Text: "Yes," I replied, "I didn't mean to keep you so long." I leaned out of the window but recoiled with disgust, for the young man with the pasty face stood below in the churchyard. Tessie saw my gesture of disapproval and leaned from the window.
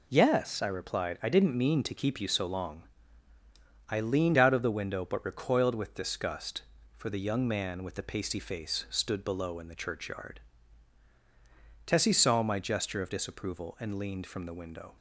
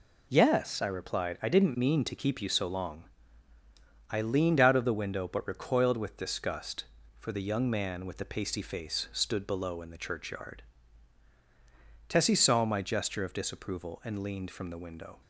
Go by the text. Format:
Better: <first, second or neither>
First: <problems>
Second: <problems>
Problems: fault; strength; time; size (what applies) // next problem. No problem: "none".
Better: neither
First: none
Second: none